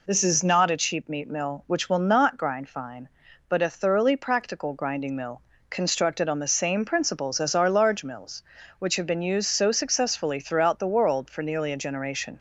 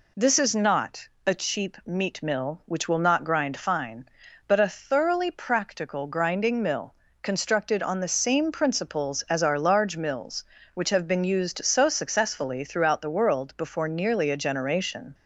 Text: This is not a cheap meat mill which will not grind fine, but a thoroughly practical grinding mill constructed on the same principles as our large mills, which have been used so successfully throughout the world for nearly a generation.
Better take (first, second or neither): first